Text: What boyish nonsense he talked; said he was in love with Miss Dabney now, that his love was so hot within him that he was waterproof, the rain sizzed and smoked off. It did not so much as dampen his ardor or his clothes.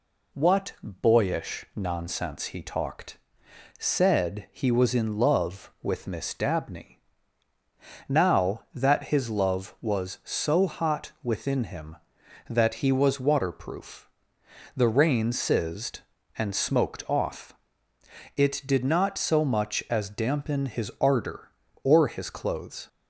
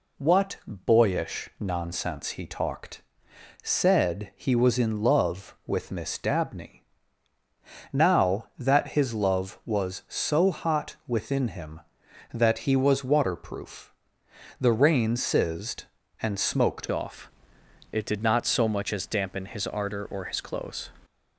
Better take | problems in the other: first | pauses between "Dabney" and "now"; at 6.7 s; 1.1 s long; also in the first // changes voice at "off"; from 16.9 s on; 3.9 s long

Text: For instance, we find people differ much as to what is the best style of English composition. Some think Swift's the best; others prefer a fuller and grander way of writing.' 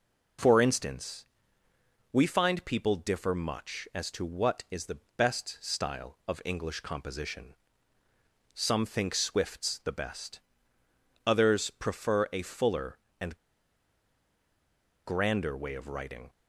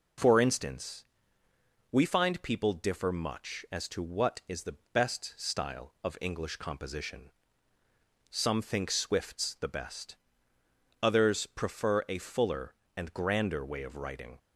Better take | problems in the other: second | pauses between "the" and "best"; slight; at 4.9 s; 0.18 s long; slight in the second // pauses between "and" and "grander"; strong; at 13.3 s; 1.6 s long

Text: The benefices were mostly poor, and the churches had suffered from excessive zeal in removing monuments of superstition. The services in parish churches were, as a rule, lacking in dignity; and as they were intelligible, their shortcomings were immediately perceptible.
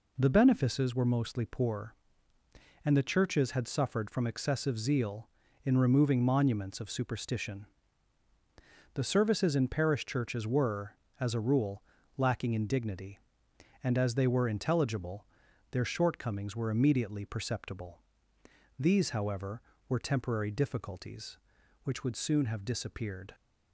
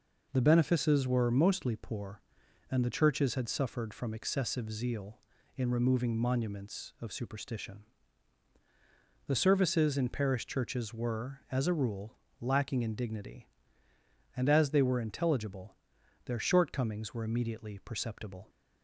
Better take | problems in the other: second | goes on to say "These however were temporary difficulties which would soon have disappeared"; strong; from 18.7 s on; 4.5 s long

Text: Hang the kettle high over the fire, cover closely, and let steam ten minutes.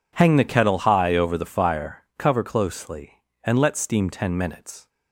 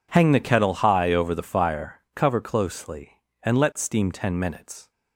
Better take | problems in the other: neither | none

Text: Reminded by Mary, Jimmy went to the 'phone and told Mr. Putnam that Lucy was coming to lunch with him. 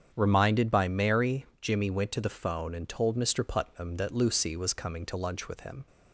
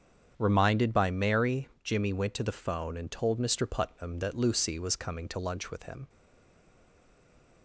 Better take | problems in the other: first | starts louder than the rest; strong; until 1.3 s; 8 dB; strong in the first // stays silent after the last word; noticeable; from 6.0 s on; 1.6 s long

